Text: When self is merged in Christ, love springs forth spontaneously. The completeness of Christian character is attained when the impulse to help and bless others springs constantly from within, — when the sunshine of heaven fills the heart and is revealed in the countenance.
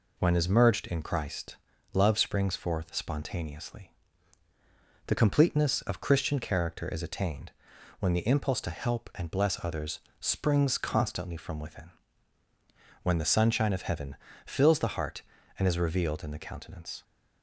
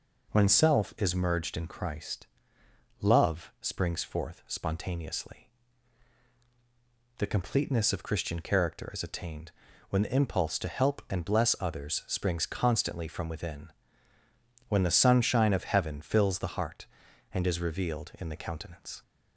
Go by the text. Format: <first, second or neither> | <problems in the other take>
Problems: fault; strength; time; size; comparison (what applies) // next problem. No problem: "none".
second | skips "self"; at 0.3 s // pauses between "attained" and "when"; noticeable; at 7.5 s; 0.48 s long; also in the second // pauses between "others" and "springs"; slight; at 9.9 s; 0.22 s long // pauses between "heaven" and "fills"; slight; at 14.1 s; 0.30 s long